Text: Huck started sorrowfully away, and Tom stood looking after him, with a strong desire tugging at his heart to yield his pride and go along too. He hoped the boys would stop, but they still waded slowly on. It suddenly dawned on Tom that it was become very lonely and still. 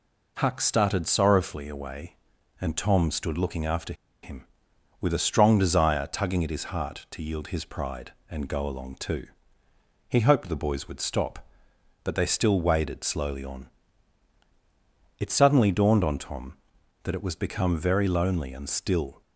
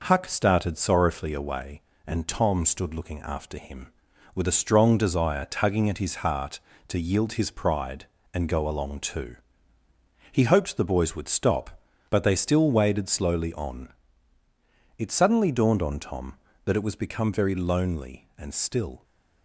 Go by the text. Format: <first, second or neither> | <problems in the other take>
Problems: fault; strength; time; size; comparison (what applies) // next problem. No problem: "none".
second | pauses between "after" and "him"; slight; at 3.9 s; 0.29 s long